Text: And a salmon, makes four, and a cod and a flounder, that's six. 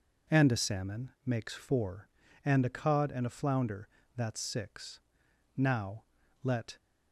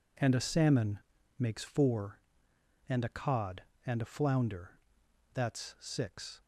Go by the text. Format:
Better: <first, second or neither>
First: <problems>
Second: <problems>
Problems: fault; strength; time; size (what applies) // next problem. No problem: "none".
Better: second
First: goes on to say "Now let"; noticeable; from 5.5 s on; 1.2 s long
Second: none